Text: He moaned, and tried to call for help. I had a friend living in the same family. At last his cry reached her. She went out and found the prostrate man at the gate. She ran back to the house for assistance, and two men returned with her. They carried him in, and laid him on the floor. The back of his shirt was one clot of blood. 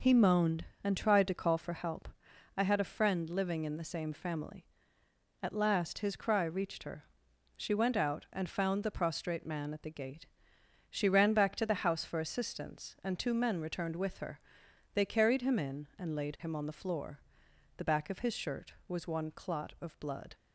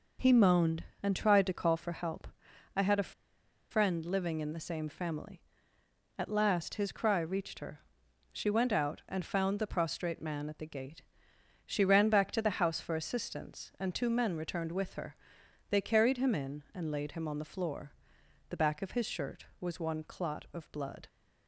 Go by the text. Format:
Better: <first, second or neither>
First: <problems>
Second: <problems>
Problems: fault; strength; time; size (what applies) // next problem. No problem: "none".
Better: first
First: none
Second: pauses between "a" and "friend"; noticeable; at 3.1 s; 0.58 s long